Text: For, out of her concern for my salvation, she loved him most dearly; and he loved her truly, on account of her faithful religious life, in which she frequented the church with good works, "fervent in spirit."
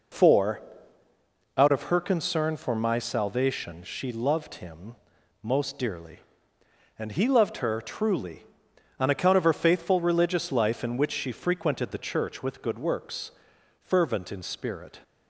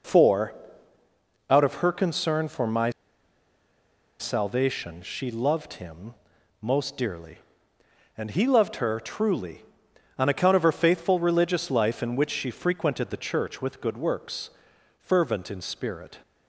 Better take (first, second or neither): first